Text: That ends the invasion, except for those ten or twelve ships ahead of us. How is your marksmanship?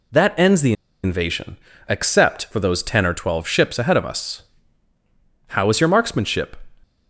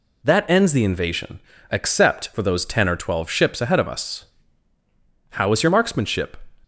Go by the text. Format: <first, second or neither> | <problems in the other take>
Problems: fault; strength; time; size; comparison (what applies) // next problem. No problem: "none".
second | pauses between "the" and "invasion"; slight; at 0.7 s; 0.31 s long